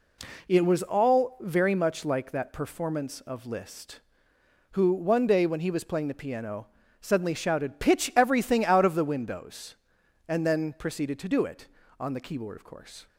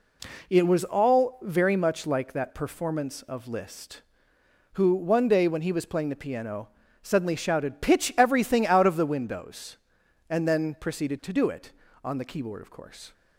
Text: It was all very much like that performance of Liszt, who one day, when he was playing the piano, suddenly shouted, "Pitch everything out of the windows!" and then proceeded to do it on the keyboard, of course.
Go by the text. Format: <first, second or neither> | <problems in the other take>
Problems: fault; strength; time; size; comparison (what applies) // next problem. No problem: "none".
neither | none